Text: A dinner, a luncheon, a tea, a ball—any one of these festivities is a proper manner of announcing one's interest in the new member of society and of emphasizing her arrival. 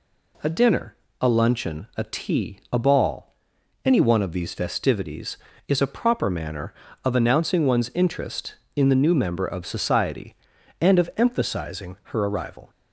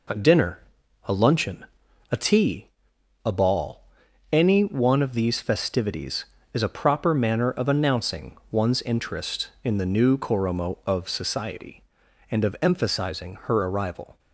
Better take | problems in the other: first | pauses between "announcing" and "one's"; slight; at 8.3 s; 0.16 s long // says "koromo" for "member"; at 10.1 s

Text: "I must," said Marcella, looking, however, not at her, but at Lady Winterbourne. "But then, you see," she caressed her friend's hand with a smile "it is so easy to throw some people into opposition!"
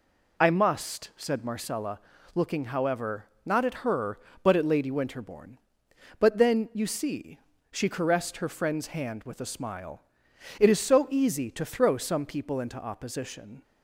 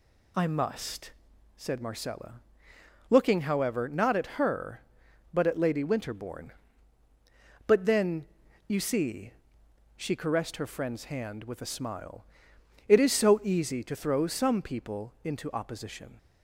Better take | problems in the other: neither | pauses between "smile" and "it"; noticeable; the same in both

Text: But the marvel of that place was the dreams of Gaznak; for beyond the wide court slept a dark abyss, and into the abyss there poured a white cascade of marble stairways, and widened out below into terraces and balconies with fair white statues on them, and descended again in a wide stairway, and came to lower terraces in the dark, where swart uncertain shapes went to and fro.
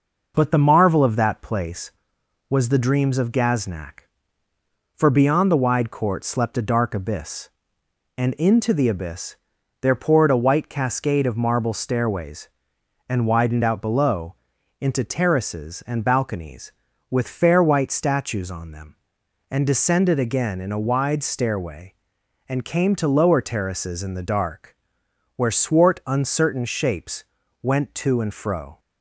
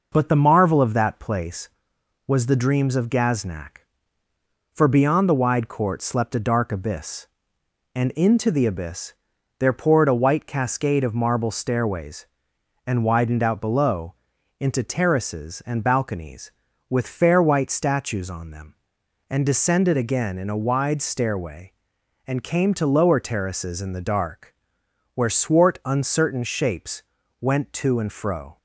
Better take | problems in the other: neither | pauses between "abyss" and "there"; the same in both // pauses between "below" and "into"; noticeable; the same in both // pauses between "shapes" and "went"; the same in both

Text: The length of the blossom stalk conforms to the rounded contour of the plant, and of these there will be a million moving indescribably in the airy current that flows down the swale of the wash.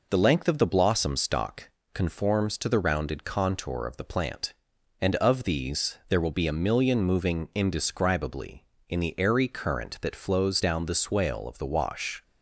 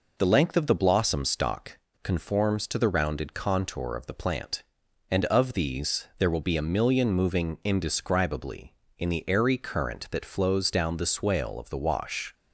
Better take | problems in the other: neither | pauses between "stalk" and "conforms"; slight; the same in both

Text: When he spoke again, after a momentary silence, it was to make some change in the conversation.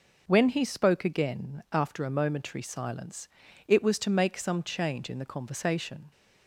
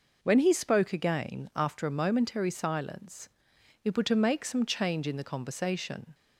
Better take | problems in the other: first | says "were" for "was"; at 3.9 s

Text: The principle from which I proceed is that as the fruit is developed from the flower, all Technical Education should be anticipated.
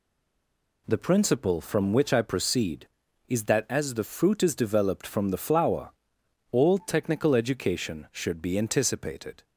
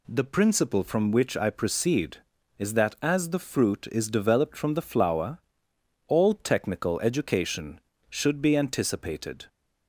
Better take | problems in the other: second | stays silent before the first word; slight; until 0.8 s; 0.8 s long

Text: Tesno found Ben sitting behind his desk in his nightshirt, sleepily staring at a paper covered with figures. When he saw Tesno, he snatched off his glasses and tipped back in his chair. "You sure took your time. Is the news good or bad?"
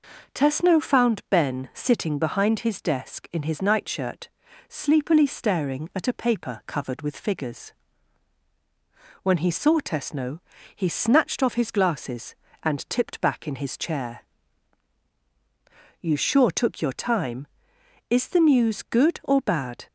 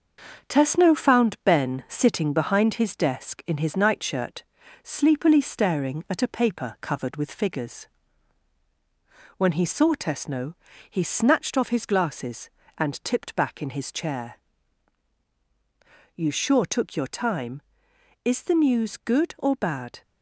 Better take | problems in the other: first | gets quieter; noticeable; throughout; 5.5 dB

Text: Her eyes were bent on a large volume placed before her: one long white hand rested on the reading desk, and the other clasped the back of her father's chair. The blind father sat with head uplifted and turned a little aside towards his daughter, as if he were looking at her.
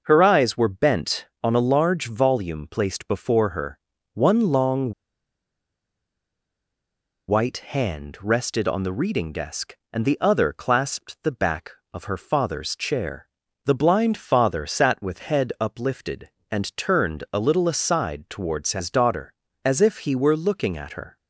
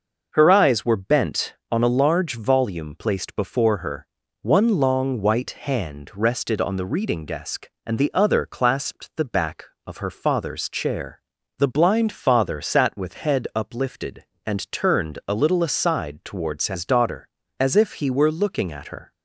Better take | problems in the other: second | pauses between "long" and "white"; strong; at 4.9 s; 2.3 s long

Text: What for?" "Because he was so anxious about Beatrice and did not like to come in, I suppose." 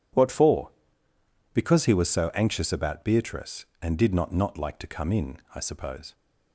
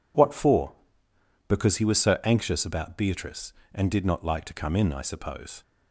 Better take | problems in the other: second | says "not" twice; at 4.3 s

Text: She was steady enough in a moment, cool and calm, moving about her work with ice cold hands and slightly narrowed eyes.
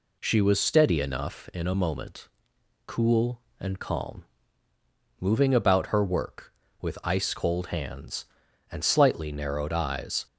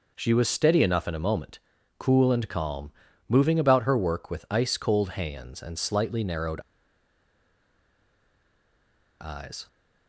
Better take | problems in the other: first | pauses between "narrowed" and "eyes"; strong; at 6.6 s; 2.5 s long

